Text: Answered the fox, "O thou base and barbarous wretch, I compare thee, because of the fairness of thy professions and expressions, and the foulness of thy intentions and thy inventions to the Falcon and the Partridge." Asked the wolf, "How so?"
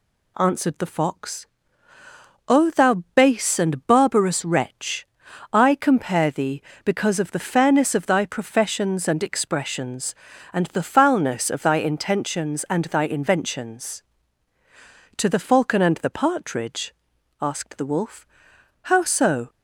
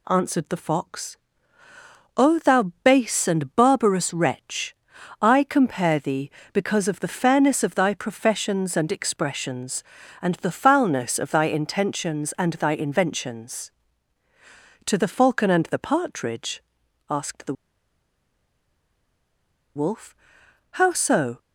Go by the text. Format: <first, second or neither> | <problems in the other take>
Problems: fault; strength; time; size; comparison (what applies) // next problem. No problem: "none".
first | pauses between "the" and "wolf"; strong; at 17.5 s; 2.2 s long